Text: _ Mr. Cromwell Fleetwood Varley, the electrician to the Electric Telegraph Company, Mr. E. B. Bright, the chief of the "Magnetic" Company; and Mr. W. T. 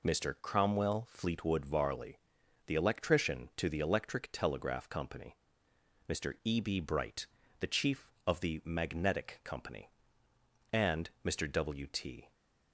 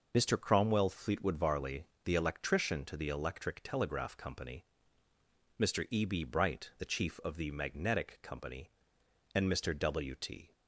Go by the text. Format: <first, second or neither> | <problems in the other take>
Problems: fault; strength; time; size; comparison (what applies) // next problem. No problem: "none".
neither | none